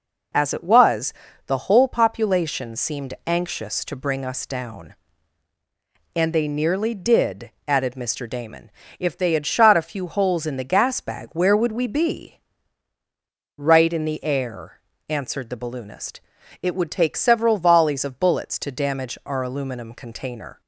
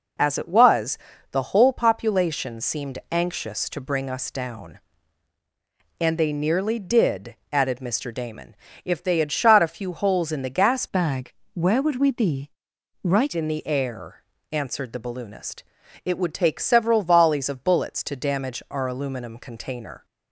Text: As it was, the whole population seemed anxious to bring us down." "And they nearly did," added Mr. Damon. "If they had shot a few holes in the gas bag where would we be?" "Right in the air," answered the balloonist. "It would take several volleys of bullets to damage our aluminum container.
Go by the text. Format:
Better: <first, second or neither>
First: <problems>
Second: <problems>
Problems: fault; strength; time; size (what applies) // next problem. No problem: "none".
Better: first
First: none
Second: changes voice from "bag" to "Right"; from 10.8 to 13.3 s; 2.5 s long // pauses between "bag" and "where"; slight; at 11.3 s; 0.22 s long